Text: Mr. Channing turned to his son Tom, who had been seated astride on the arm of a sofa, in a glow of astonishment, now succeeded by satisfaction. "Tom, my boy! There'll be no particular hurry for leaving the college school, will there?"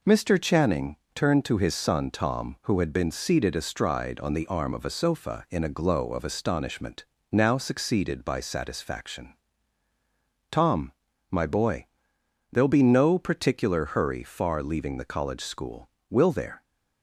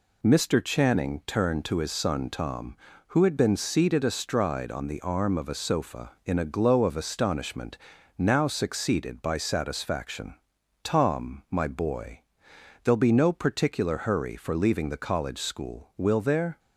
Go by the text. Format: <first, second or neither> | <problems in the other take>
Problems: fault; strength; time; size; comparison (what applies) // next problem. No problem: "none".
second | pauses between "Channing" and "turned"; slight; at 0.9 s; 0.18 s long // says "far" for "for"; at 14.2 s